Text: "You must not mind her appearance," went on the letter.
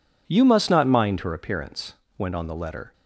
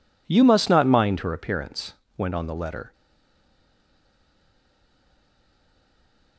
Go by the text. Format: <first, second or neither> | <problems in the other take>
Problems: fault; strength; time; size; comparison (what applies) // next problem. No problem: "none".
first | stays silent after the last word; strong; from 2.9 s on; 3.4 s long